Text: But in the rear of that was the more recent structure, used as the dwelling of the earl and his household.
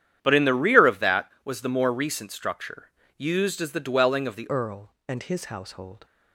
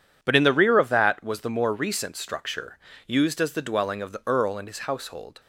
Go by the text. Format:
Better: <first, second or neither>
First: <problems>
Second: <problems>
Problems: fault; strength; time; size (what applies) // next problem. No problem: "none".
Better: second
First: starts louder than the rest; strong; until 1.2 s; 10 dB // changes voice at "earl"; from 4.4 s on; 1.6 s long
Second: none